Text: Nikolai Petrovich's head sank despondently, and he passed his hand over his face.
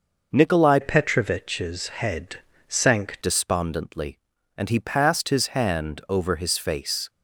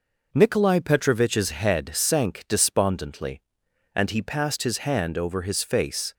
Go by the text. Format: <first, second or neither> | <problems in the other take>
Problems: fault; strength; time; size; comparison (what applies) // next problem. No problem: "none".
second | changes voice from "Petrovich's" to "sank"; from 0.8 to 3.1 s; 2.3 s long // pauses between "head" and "sank"; slight; at 2.3 s; 0.32 s long